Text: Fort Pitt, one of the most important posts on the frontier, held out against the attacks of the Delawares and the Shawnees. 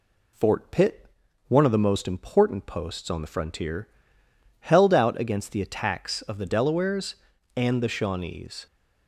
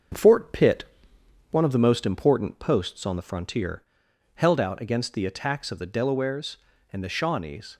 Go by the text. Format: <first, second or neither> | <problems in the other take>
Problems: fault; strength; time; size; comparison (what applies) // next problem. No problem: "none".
first | gets quieter; slight; throughout; 3 dB